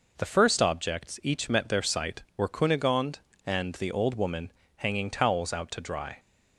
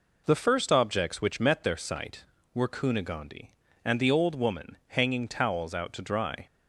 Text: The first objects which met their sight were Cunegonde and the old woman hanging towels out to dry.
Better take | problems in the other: second | says "each" for "which"; at 1.2 s // pauses between "woman" and "hanging"; slight; at 4.5 s; 0.26 s long

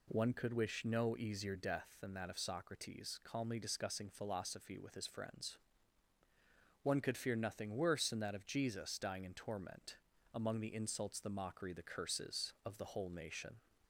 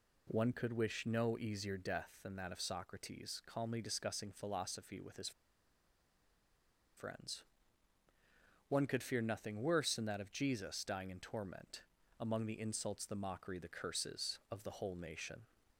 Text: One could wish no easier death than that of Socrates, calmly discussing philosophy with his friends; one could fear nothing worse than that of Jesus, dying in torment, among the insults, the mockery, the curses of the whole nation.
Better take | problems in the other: first | pauses between "his" and "friends"; strong; at 5.3 s; 1.6 s long

